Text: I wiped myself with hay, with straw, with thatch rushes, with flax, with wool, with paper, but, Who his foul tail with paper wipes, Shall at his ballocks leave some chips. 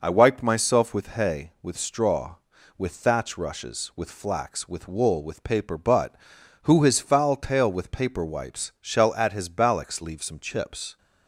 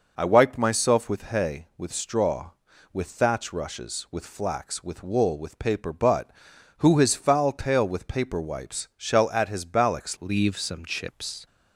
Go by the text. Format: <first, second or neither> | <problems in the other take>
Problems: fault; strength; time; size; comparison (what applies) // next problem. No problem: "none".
first | changes voice at "leave"; from 10.2 s on; 1.2 s long